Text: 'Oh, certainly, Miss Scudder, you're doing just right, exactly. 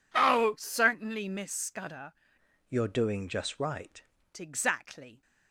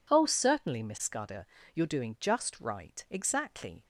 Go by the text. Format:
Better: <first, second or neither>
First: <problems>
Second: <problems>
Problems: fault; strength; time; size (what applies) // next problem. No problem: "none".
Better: second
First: changes voice from "you're" to "right"; from 2.6 to 4.0 s; 1.4 s long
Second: none